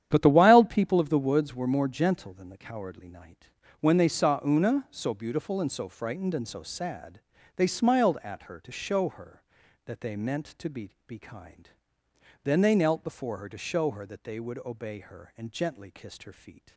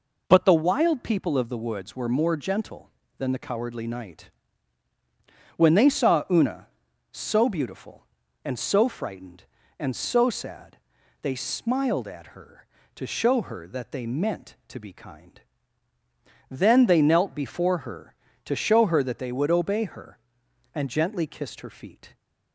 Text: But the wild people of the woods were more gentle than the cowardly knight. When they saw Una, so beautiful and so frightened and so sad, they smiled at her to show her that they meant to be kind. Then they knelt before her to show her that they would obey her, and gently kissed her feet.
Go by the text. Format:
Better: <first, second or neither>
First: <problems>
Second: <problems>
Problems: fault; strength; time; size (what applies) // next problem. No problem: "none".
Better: second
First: starts louder than the rest; strong; until 1.1 s; 10 dB // says "be" twice; at 11.0 s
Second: none